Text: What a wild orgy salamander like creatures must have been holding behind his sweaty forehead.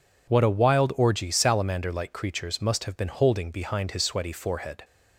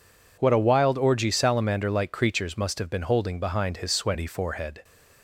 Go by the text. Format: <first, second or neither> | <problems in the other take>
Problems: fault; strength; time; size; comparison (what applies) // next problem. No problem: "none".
neither | none